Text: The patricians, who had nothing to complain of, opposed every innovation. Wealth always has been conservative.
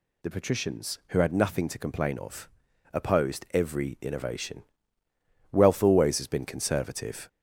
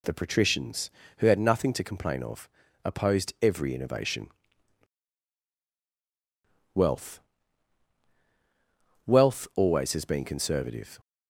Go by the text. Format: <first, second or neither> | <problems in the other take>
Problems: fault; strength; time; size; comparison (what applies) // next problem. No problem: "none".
first | says "Wealth" twice; at 9.0 s